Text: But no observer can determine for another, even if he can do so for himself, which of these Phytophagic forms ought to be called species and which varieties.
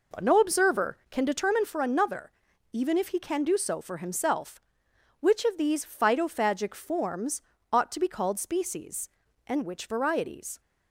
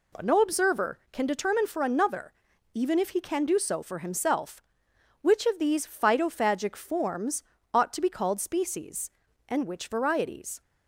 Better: second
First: starts louder than the rest; noticeable; until 1.7 s; 4.5 dB // pauses between "forms" and "ought"; slight; at 7.3 s; 0.32 s long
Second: pauses between "forms" and "ought"; slight; at 7.4 s; 0.32 s long

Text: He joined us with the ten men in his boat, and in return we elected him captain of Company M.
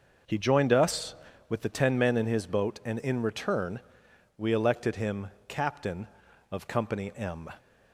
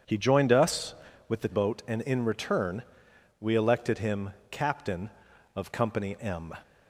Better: first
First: pauses between "return" and "we"; noticeable; at 3.7 s; 0.58 s long // pauses between "him" and "captain"; slight; at 5.2 s; 0.20 s long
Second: skips "ten men in his"; at 1.4 s // pauses between "return" and "we"; noticeable; at 2.8 s; 0.58 s long // pauses between "him" and "captain"; slight; at 4.3 s; 0.20 s long

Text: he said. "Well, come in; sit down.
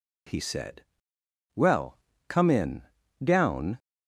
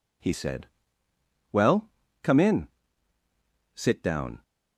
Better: second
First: skips "sit"; at 3.0 s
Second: none

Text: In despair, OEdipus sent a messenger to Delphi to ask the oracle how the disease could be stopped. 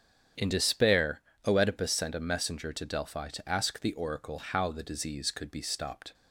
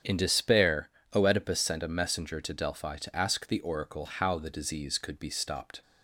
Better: neither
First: starts louder than the rest; strong; until 1.6 s; 8 dB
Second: starts louder than the rest; strong; until 1.2 s; 8 dB

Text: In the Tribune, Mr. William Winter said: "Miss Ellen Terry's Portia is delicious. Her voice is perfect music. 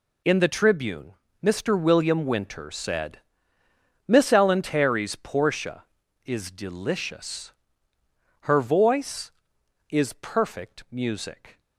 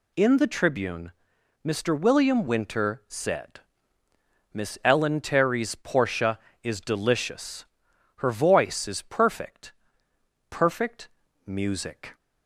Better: first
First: none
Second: says "perfect" twice; at 10.4 s

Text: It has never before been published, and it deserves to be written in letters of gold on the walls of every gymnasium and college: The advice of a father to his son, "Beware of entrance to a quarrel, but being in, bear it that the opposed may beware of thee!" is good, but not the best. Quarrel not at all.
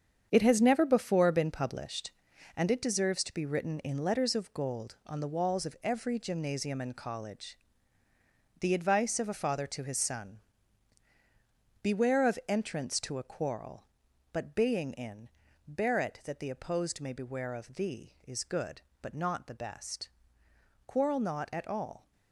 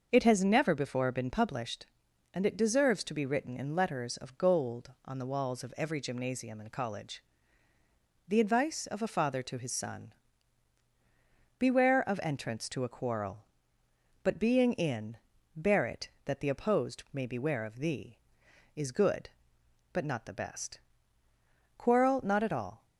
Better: second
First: gets quieter; strong; throughout; 9.5 dB // starts louder than the rest; strong; until 1.3 s; 7.5 dB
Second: starts louder than the rest; noticeable; until 1.1 s; 6 dB

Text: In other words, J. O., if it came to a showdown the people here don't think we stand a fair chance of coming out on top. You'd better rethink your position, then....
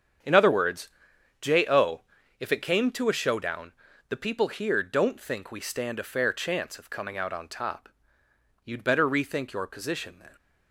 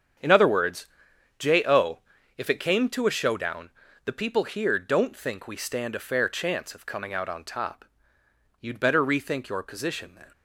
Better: neither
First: starts louder than the rest; strong; until 1.7 s; 8 dB // pauses between "showdown" and "the"; at 3.7 s; 0.38 s long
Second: starts louder than the rest; strong; until 1.7 s; 7.5 dB // pauses between "showdown" and "the"; at 3.6 s; 0.36 s long

